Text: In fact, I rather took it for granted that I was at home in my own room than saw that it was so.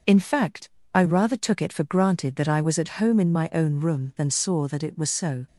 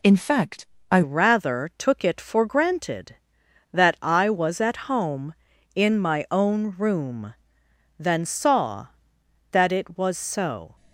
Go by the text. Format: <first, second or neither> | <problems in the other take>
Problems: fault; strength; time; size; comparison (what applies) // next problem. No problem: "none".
first | changes voice at "rather"; from 1.0 s on; 9.7 s long